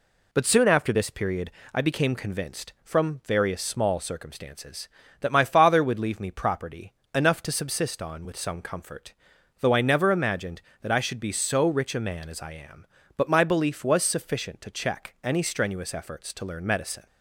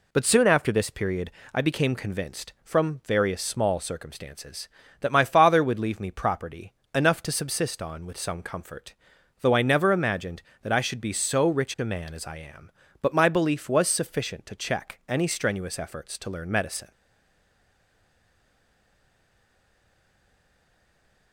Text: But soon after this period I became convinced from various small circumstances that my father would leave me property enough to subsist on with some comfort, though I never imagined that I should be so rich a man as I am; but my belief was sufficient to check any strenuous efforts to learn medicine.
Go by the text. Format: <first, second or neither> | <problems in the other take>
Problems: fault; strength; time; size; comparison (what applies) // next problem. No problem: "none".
first | pauses between "period" and "I"; slight; at 1.3 s; 0.22 s long; slight in the first // pauses between "property" and "enough"; slight; at 6.7 s; 0.22 s long; slight in the first // stays silent after the last word; strong; from 16.9 s on; 4.4 s long